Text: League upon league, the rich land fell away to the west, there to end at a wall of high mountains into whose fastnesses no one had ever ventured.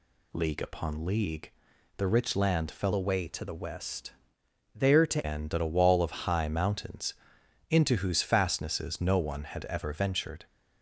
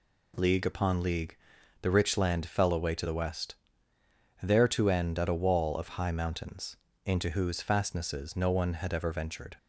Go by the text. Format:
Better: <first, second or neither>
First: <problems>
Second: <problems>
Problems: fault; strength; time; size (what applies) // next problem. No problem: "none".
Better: second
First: changes voice from "away" to "to"; from 2.9 to 5.2 s; 2.3 s long // pauses between "mountains" and "into"; noticeable; at 7.1 s; 0.56 s long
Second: pauses between "mountains" and "into"; slight; at 6.7 s; 0.30 s long